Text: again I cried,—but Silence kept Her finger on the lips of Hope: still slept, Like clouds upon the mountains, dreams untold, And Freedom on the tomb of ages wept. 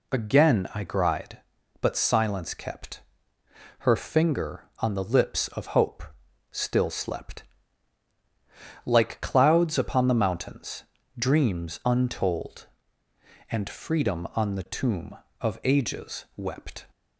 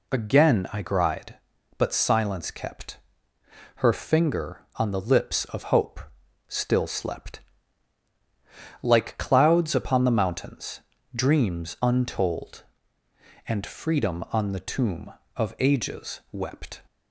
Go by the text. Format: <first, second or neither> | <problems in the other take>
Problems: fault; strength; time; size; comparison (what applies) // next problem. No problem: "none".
neither | pauses between "kept" and "Her"; noticeable; the same in both